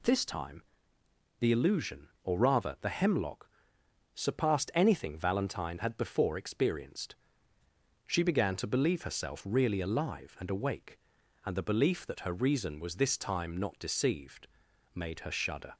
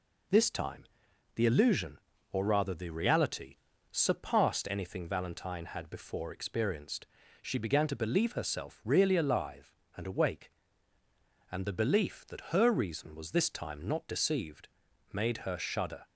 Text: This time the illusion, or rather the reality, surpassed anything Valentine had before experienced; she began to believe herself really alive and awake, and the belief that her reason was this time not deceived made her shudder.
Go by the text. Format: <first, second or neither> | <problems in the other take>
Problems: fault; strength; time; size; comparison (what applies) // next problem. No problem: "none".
second | pauses between "time" and "the"; noticeable; at 0.6 s; 0.76 s long; noticeable in the second // says "hemlock" for "reality"; at 2.8 s // pauses between "deceived" and "made"; noticeable; at 14.4 s; 0.48 s long; also in the second